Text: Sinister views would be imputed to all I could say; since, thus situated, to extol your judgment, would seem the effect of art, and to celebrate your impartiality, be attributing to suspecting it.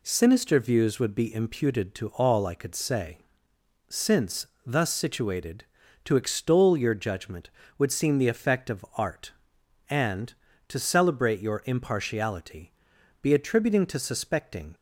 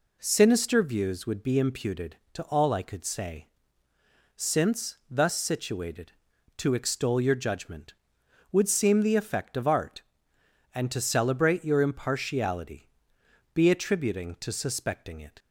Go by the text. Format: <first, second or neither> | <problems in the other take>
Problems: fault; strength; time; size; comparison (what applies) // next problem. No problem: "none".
second | stops before "it"; at 14.7 s